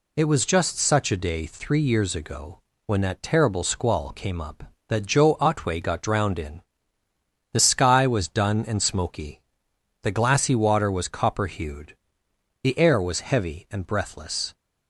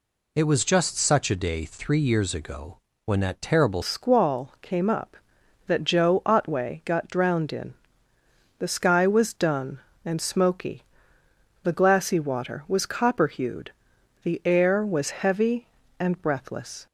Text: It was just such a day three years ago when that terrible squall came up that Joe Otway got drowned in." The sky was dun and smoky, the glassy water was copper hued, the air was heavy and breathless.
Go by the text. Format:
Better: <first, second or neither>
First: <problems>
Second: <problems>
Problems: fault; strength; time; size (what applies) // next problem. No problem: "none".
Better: first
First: pauses between "ago" and "when"; slight; at 2.5 s; 0.26 s long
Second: pauses between "ago" and "when"; slight; at 2.7 s; 0.26 s long // changes voice at "squall"; from 3.8 s on; 13.0 s long